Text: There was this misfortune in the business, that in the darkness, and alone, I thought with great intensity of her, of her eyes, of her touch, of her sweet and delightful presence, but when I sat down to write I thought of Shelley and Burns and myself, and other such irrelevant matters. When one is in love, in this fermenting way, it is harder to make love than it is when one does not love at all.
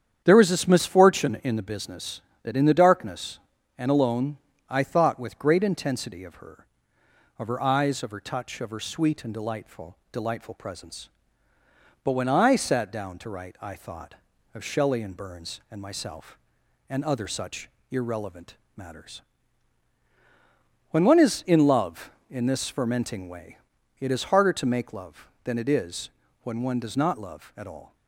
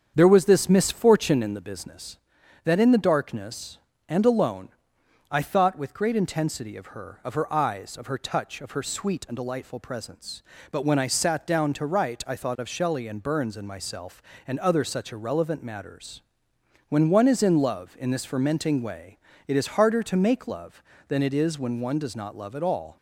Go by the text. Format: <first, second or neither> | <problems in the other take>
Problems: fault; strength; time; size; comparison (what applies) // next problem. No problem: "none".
second | starts louder than the rest; strong; until 1.2 s; 9 dB; strong in the second // says "delightful" twice; at 10.1 s // pauses between "such" and "irrelevant"; slight; at 17.6 s; 0.20 s long // pauses between "irrelevant" and "matters"; slight; at 18.5 s; 0.20 s long // pauses between "is" and "when"; slight; at 26.0 s; 0.32 s long